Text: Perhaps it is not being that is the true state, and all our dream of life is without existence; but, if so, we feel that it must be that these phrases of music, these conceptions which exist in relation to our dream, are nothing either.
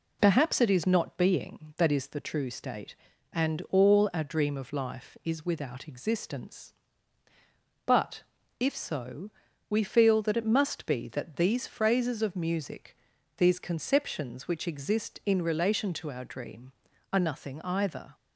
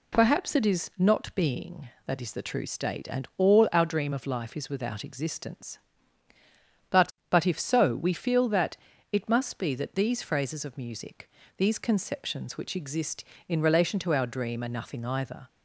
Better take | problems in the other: first | says "but" twice; at 7.2 s // pauses between "that" and "it"; at 8.7 s; 0.38 s long

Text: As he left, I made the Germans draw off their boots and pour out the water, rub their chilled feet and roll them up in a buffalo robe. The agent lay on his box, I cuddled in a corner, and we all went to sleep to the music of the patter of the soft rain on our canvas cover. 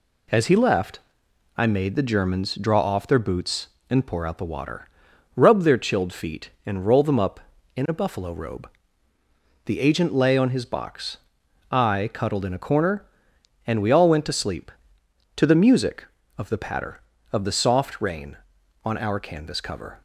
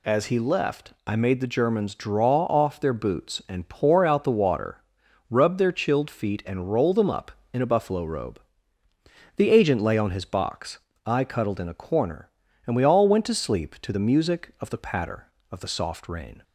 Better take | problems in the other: first | stops before "on our canvas cover"; at 16.4 s

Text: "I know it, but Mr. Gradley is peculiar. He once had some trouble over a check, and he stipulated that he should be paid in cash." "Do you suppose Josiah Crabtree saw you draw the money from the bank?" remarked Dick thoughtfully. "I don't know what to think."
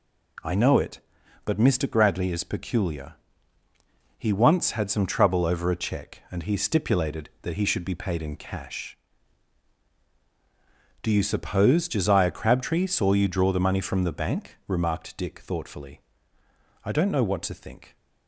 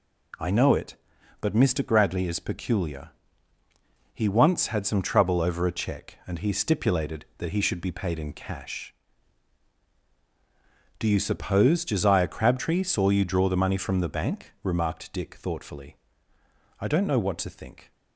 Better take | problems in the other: neither | none

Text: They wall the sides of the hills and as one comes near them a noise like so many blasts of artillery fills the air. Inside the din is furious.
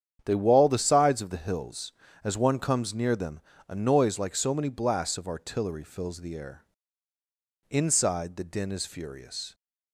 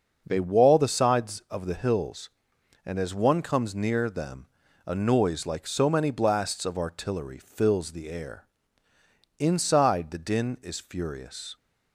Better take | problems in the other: second | starts louder than the rest; strong; until 1.2 s; 8.5 dB; also in the second // skips "and"; at 2.0 s // pauses between "them" and "a"; slight; at 3.4 s; 0.28 s long; also in the second

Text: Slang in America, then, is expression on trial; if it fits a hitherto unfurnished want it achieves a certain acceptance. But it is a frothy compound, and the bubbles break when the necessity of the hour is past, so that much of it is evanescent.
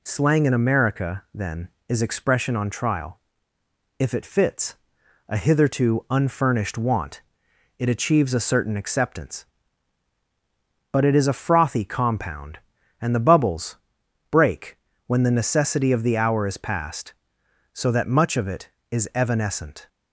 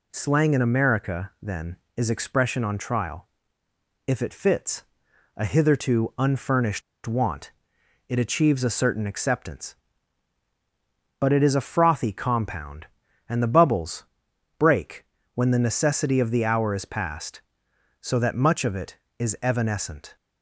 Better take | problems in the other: first | pauses between "fits" and "a"; noticeable; at 4.8 s; 0.54 s long; noticeable in the first // pauses between "unfurnished" and "want"; slight; at 6.8 s; 0.23 s long // pauses between "want" and "it"; noticeable; at 7.5 s; 0.56 s long; noticeable in the first // pauses between "bubbles" and "break"; noticeable; at 14.0 s; 0.52 s long; noticeable in the first // pauses between "break" and "when"; slight; at 15.0 s; 0.30 s long; slight in the first

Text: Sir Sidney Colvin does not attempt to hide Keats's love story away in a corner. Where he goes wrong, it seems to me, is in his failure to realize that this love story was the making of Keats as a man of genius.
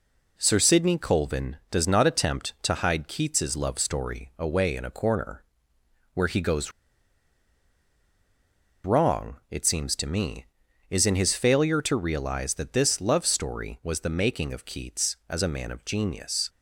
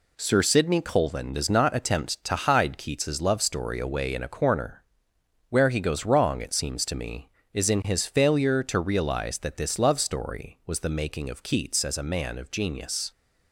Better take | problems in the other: second | pauses between "goes" and "wrong"; strong; at 6.7 s; 2.1 s long

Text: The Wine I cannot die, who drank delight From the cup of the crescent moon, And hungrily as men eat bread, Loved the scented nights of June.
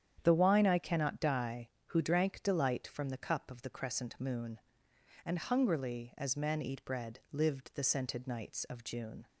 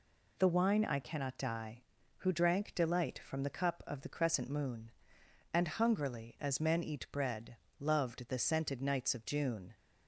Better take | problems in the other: second | starts louder than the rest; strong; until 1.2 s; 9 dB // says "Lived" for "Loved"; at 7.3 s

